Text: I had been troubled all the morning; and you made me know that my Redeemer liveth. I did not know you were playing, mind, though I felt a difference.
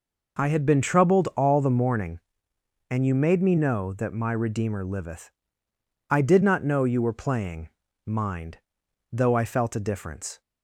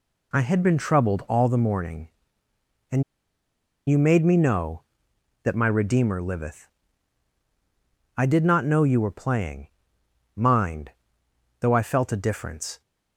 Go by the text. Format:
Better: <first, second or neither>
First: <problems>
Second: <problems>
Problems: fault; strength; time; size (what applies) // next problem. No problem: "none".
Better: first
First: none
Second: pauses between "and" and "you"; noticeable; at 3.0 s; 0.85 s long